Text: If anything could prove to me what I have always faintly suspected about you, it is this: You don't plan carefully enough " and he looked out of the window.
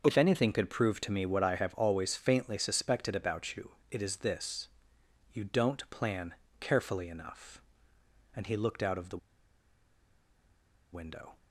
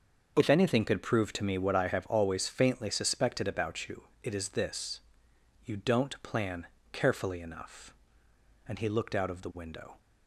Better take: second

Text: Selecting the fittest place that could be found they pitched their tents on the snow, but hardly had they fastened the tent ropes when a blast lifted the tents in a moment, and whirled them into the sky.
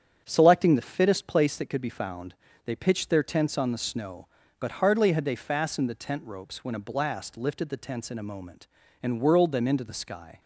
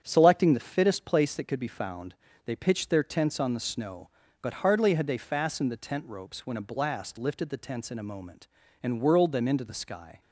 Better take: neither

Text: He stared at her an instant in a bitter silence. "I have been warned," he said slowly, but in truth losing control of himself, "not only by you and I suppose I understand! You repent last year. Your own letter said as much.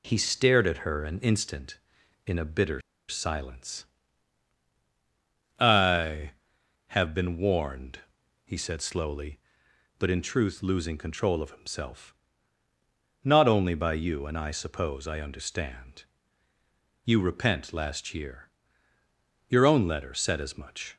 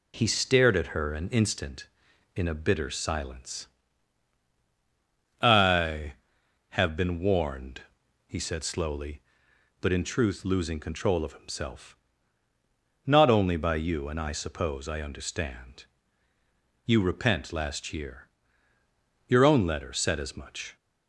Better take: second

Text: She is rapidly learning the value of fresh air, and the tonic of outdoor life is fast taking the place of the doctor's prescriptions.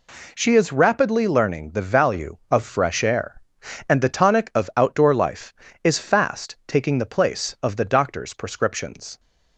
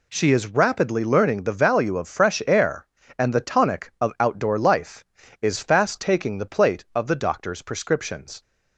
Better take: first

